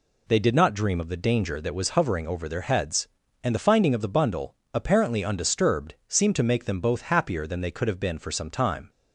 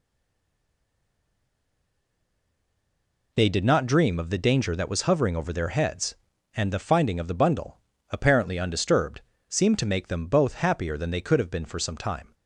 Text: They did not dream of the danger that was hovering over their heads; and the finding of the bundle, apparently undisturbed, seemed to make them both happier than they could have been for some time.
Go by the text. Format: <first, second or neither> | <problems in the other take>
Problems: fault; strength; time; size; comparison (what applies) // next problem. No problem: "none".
first | stays silent before the first word; strong; until 3.3 s; 3.3 s long